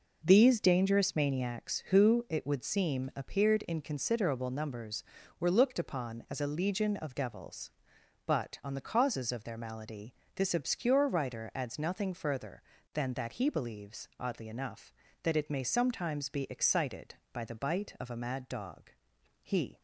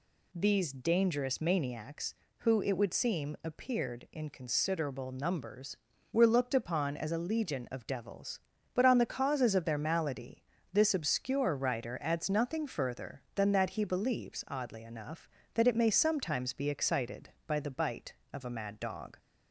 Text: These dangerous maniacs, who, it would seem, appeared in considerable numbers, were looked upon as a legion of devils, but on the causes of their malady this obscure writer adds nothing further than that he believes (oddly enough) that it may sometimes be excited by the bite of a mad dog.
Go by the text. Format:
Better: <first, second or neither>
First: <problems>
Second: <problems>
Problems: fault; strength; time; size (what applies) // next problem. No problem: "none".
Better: second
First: pauses between "malady" and "this"; slight; at 10.1 s; 0.22 s long // goes on to say "He"; slight; from 19.4 s on; 0.38 s long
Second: pauses between "malady" and "this"; slight; at 10.4 s; 0.30 s long